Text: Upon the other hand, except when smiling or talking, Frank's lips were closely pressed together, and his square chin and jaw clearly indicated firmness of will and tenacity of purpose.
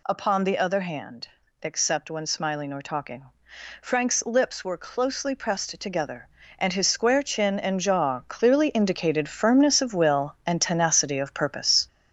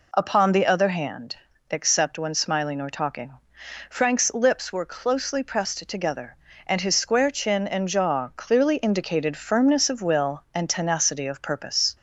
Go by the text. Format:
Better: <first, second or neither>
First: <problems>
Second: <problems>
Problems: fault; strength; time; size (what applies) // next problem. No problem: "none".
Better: second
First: gets louder; throughout; 6.5 dB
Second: none